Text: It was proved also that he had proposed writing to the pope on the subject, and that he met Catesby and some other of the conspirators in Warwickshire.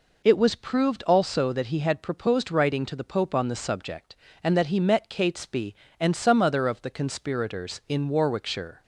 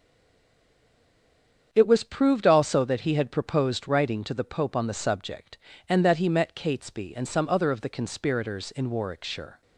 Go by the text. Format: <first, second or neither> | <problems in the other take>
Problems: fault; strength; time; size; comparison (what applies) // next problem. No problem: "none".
first | stays silent before the first word; noticeable; until 1.7 s; 1.7 s long // starts louder than the rest; strong; until 2.7 s; 7.5 dB